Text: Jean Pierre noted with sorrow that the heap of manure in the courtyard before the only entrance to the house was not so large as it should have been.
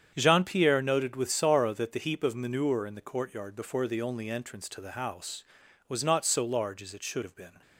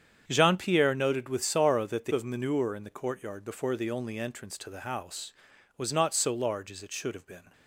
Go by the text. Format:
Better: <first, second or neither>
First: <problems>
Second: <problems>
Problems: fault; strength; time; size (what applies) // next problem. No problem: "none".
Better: first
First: starts louder than the rest; strong; until 1.1 s; 8 dB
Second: starts louder than the rest; strong; until 1.2 s; 8 dB // skips "heap"; at 2.1 s